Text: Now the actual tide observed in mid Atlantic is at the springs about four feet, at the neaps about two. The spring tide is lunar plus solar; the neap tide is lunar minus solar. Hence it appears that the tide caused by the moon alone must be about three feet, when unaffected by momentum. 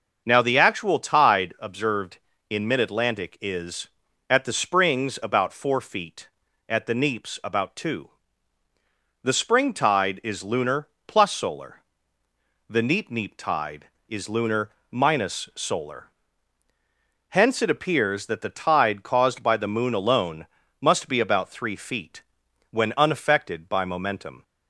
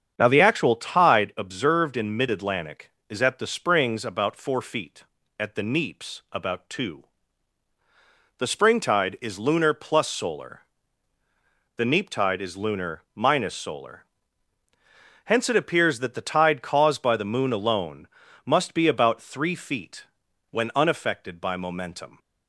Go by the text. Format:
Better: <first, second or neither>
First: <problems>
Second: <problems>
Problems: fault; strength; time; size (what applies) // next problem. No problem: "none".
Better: second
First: starts louder than the rest; until 1.2 s; 6.5 dB // pauses between "lunar" and "plus"; slight; at 10.8 s; 0.20 s long // says "neap" twice; at 13.0 s // pauses between "lunar" and "minus"; slight; at 14.7 s; 0.20 s long // pauses between "alone" and "must"; slight; at 20.4 s; 0.34 s long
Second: starts louder than the rest; strong; until 1.1 s; 7.5 dB // pauses between "alone" and "must"; at 18.0 s; 0.38 s long